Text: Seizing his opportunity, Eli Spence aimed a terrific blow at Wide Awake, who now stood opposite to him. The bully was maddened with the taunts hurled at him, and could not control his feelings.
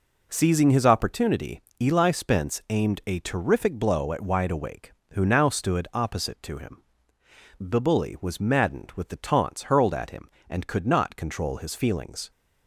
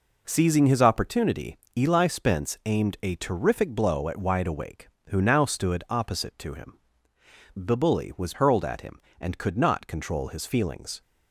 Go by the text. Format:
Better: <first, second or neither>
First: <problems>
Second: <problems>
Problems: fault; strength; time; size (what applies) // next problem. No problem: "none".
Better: first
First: none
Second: skips "maddened with the taunts"; at 8.3 s